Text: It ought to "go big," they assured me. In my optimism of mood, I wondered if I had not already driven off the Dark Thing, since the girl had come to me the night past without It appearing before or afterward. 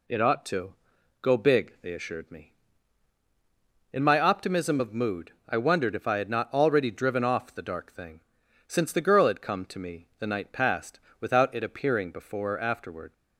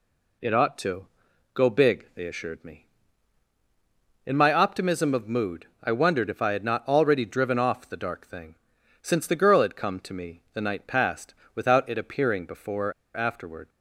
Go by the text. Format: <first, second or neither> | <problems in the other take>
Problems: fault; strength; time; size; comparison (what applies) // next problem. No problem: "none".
first | pauses between "to" and "go"; noticeable; at 1.0 s; 0.46 s long; noticeable in the first // pauses between "past" and "without"; slight; at 11.3 s; 0.22 s long; slight in the first // pauses between "or" and "afterward"; slight; at 12.9 s; 0.24 s long